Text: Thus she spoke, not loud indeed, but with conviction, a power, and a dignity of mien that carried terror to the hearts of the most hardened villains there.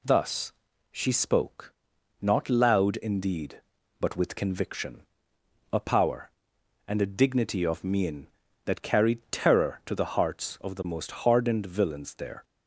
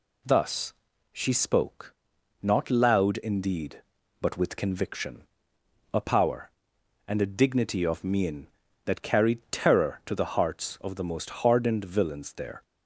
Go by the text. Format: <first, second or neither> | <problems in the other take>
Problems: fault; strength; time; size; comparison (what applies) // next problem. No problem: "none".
neither | pauses between "Thus" and "she"; the same in both